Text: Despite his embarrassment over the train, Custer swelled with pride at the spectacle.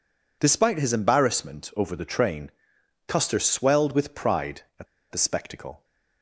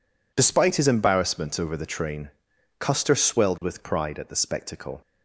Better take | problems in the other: second | pauses between "at" and "the"; slight; at 4.8 s; 0.25 s long

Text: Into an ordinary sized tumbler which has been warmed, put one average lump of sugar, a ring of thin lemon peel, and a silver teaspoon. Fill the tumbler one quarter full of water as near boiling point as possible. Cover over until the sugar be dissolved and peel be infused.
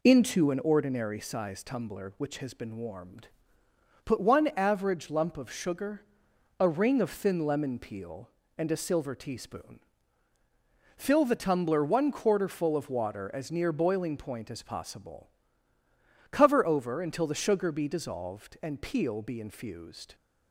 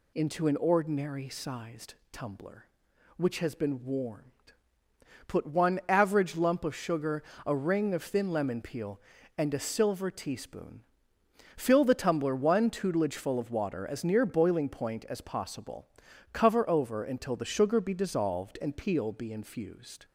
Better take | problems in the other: first | pauses between "sized" and "tumbler"; slight; at 1.9 s; 0.16 s long // says "tutelage" for "quarter"; at 12.6 s

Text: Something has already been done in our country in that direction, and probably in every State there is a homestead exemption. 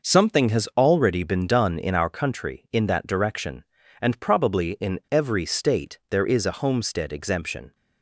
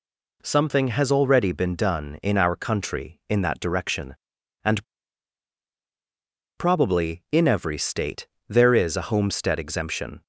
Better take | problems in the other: first | pauses between "and" and "probably"; strong; at 4.8 s; 1.7 s long // pauses between "State" and "there"; slight; at 8.2 s; 0.20 s long

